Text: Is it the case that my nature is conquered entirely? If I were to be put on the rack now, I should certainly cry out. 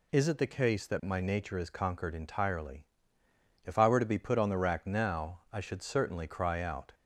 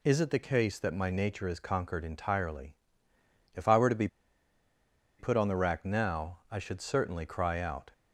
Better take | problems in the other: first | pauses between "be" and "put"; at 4.0 s; 1.1 s long

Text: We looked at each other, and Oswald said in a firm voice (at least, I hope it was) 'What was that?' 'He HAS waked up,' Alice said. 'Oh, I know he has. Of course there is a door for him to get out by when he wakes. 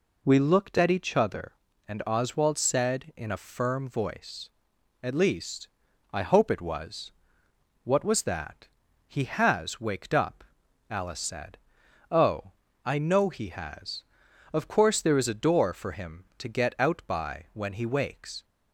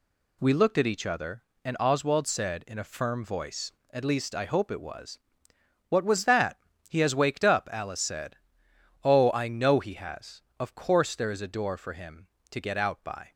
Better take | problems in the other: first | stops before "when he wakes"; at 13.3 s

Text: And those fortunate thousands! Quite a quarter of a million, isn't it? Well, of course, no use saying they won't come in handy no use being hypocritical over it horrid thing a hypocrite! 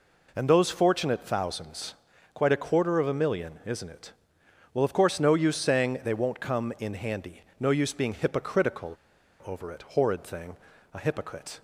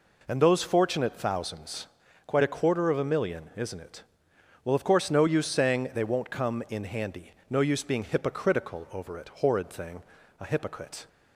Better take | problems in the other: second | pauses between "handy" and "no"; slight; at 7.4 s; 0.20 s long; slight in the second // pauses between "hypocritical" and "over"; noticeable; at 8.9 s; 0.49 s long // pauses between "thing" and "a"; slight; at 10.5 s; 0.36 s long; slight in the second

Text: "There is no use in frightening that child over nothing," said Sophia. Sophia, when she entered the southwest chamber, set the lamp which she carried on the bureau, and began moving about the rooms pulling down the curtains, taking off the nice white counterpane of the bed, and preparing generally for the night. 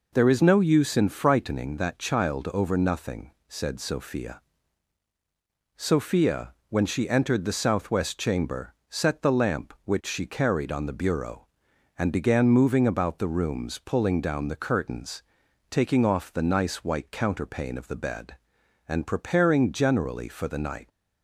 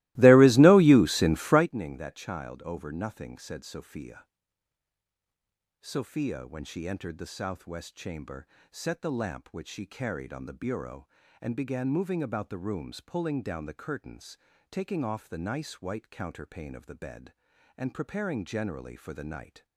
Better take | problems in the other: first | starts louder than the rest; strong; until 1.7 s; 20 dB

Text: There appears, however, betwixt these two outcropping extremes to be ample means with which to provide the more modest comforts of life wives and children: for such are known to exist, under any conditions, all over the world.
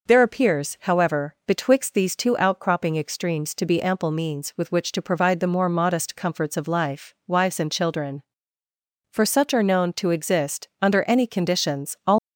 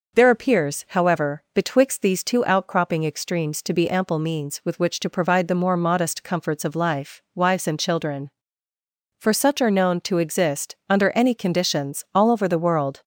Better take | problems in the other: second | stops before "over the world"; at 12.1 s

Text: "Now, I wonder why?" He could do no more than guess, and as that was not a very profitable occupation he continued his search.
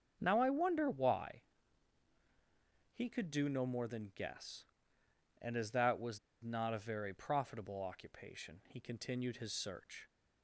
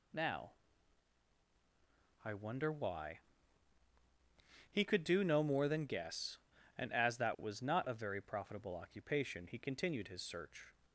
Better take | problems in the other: second | starts louder than the rest; strong; until 1.2 s; 7 dB // pauses between "was" and "not"; slight; at 6.1 s; 0.24 s long

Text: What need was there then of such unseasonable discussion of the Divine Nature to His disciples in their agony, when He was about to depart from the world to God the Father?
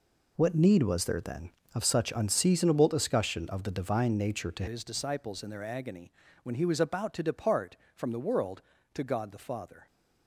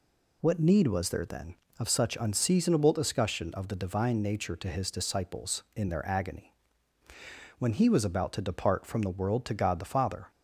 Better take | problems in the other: second | changes voice at "His"; from 4.6 s on; 5.2 s long

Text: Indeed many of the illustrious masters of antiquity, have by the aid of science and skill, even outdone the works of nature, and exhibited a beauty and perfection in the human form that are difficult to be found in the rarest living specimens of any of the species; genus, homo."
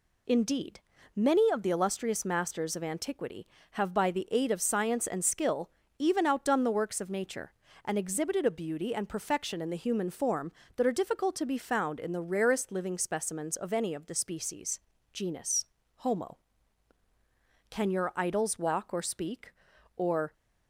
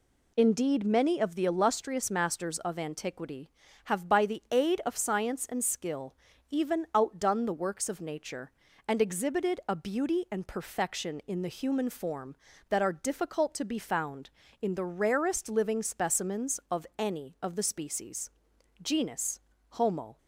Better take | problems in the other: second | pauses between "Indeed" and "many"; slight; at 0.8 s; 0.34 s long // goes on to say "Can your idols walk or speak or"; strong; from 17.6 s on; 2.6 s long

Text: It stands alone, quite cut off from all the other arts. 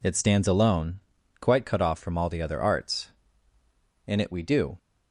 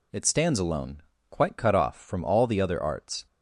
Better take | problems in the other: second | goes on to say "In it we do"; noticeable; from 4.0 s on; 0.72 s long

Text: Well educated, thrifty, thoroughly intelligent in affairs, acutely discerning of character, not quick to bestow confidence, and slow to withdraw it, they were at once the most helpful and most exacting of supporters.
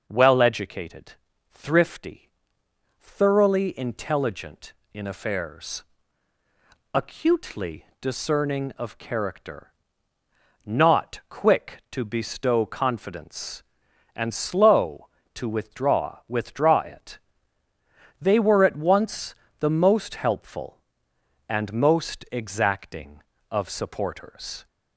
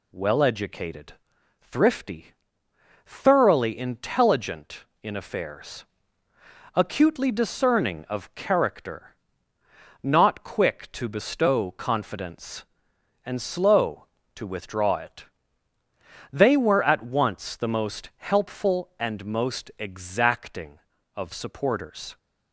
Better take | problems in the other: second | pauses between "acutely" and "discerning"; slight; at 7.8 s; 0.16 s long // says "withdraw" twice; at 16.2 s // pauses between "once" and "the"; slight; at 19.3 s; 0.24 s long

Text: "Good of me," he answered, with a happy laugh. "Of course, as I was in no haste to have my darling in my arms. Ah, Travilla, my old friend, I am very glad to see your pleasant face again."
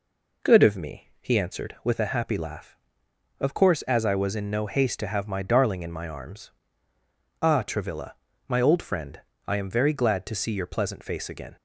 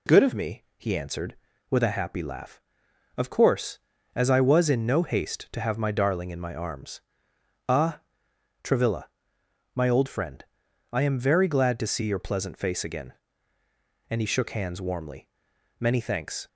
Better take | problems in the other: first | goes on to say "And he shook hands warmly Many thanks"; strong; from 14.0 s on; 2.3 s long

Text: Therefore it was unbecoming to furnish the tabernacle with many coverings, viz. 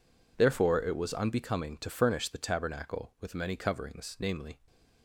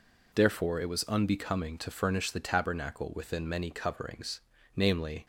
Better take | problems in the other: first | says "within" for "with"; at 3.1 s

